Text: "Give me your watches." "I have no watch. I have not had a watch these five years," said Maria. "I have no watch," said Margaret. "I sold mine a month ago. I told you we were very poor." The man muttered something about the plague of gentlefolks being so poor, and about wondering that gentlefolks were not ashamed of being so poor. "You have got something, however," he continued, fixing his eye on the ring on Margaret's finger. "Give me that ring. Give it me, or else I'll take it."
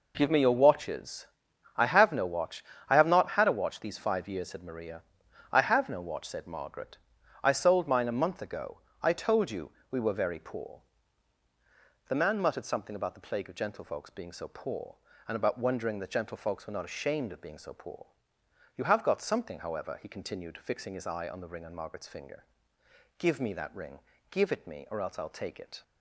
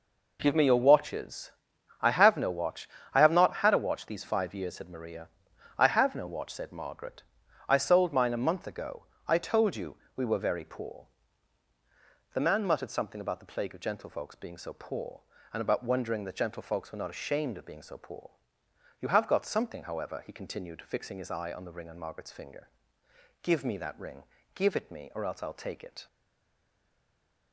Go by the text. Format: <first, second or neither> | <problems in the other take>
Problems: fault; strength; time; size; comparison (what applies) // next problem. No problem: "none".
first | pauses between "you" and "we"; slight; at 9.9 s; 0.18 s long; slight in the first // stays silent after the last word; noticeable; from 26.0 s on; 1.5 s long